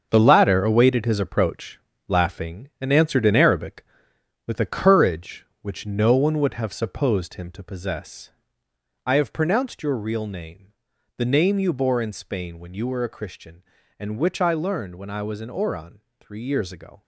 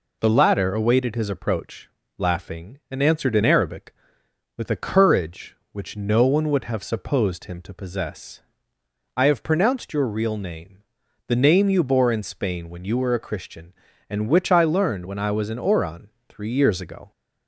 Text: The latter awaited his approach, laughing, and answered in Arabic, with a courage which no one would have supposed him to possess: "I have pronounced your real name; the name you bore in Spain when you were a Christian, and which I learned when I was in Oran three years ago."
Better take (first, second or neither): second